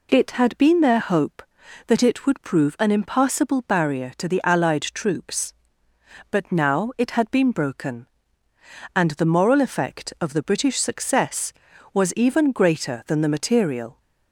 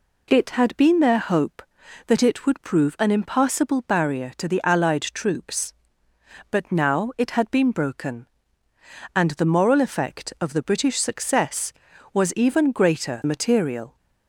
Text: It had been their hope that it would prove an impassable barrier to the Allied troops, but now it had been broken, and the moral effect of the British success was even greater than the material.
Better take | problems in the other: first | skips "than the"; at 13.2 s

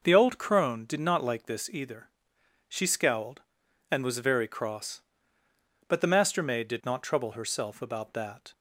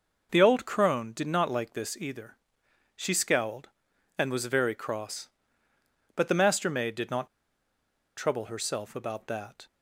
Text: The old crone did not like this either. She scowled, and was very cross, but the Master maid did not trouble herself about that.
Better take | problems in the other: first | pauses between "not" and "trouble"; noticeable; at 7.2 s; 0.89 s long

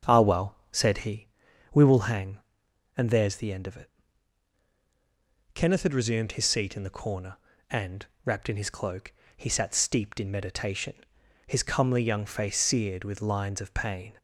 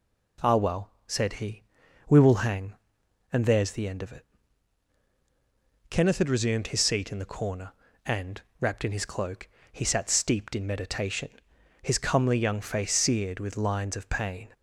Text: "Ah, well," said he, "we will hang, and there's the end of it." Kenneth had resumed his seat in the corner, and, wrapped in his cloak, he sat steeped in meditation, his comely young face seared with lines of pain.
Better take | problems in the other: second | starts louder than the rest; until 1.1 s; 7 dB

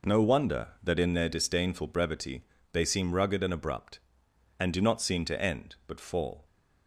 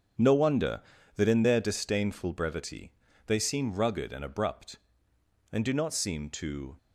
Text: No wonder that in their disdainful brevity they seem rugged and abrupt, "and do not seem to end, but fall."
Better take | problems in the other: first | starts louder than the rest; strong; until 1.5 s; 8 dB // pauses between "brevity" and "they"; slight; at 2.9 s; 0.34 s long; slight in the first // stops before "end but fall"; at 6.7 s

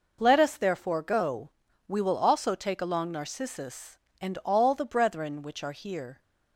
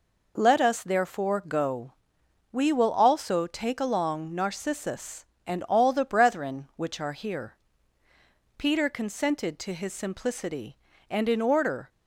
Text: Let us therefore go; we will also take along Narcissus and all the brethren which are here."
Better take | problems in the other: first | goes on to say "Peter consented to his simplicity and in order"; strong; from 8.5 s on; 3.3 s long

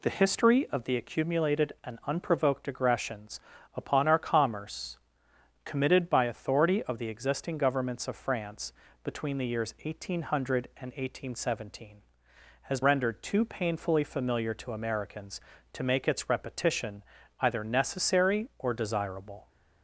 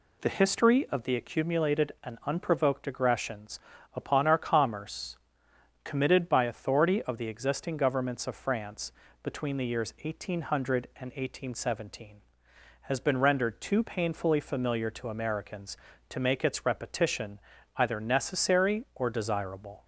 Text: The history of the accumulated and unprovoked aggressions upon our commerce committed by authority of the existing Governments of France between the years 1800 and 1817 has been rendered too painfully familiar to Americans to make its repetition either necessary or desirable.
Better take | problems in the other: second | pauses between "aggressions" and "upon"; slight; at 3.3 s; 0.36 s long; slight in the second // pauses between "commerce" and "committed"; noticeable; at 4.9 s; 0.70 s long; noticeable in the second // pauses between "France" and "between"; slight; at 8.7 s; 0.32 s long; slight in the second // skips "been"; at 12.8 s // pauses between "repetition" and "either"; at 17.0 s; 0.38 s long; also in the second

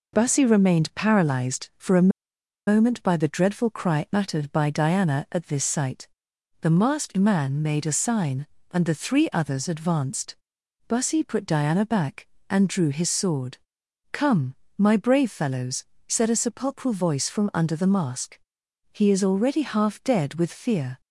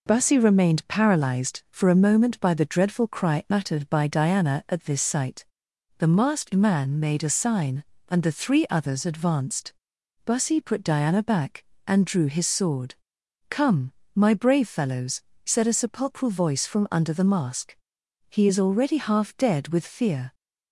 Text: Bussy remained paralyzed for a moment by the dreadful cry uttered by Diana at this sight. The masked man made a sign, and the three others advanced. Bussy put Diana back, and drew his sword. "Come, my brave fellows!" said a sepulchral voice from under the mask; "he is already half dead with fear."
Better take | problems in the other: second | pauses between "a" and "moment"; noticeable; at 2.0 s; 0.58 s long

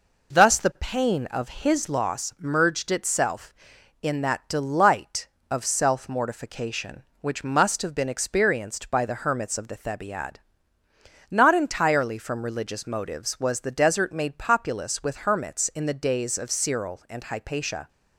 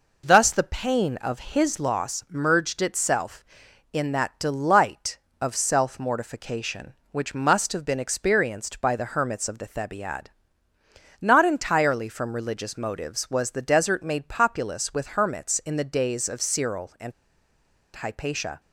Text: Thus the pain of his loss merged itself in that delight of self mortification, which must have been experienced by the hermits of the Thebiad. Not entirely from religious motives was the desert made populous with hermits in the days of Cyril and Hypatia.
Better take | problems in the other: first | pauses between "and" and "Hypatia"; noticeable; at 17.1 s; 0.83 s long

